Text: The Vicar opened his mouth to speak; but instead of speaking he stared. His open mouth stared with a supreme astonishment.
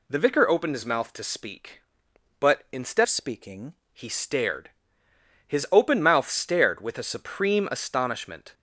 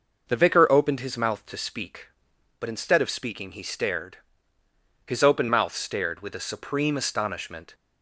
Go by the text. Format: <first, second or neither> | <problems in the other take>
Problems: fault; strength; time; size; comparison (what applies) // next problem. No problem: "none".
second | changes voice from "of" to "speaking"; from 3.0 to 3.7 s; 0.7 s long